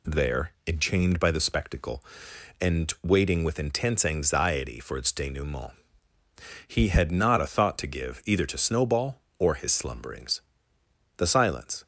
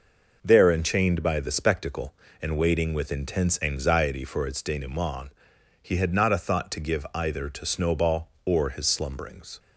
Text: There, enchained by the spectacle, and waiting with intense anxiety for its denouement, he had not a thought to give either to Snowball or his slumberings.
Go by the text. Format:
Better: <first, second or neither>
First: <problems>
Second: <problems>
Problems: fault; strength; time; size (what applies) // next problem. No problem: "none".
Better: second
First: goes on to say "The silence"; noticeable; from 11.1 s on; 0.70 s long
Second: none